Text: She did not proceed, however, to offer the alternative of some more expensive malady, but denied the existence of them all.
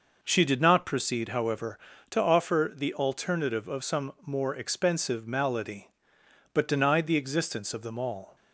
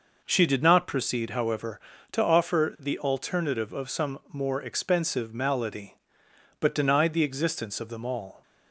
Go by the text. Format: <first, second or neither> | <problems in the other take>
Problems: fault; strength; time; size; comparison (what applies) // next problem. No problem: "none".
neither | none